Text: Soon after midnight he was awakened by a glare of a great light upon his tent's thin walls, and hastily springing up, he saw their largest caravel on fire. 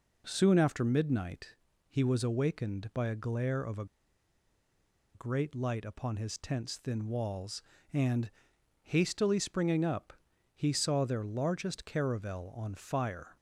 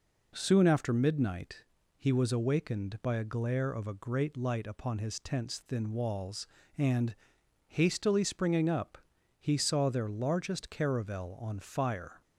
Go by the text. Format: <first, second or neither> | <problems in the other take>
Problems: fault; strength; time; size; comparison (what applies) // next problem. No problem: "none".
second | pauses between "midnight" and "he"; slight; at 1.5 s; 0.34 s long; slight in the second // pauses between "a" and "great"; strong; at 3.8 s; 1.2 s long // pauses between "and" and "hastily"; noticeable; at 8.3 s; 0.54 s long; noticeable in the second